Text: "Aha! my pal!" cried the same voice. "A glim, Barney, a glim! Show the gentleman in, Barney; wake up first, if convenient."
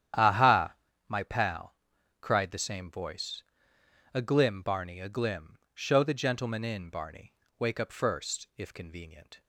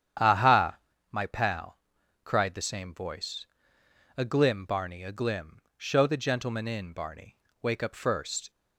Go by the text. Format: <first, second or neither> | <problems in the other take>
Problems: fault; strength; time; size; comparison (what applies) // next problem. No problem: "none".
first | starts louder than the rest; strong; until 1.5 s; 9 dB; strong in the first // stops before "if convenient"; at 8.4 s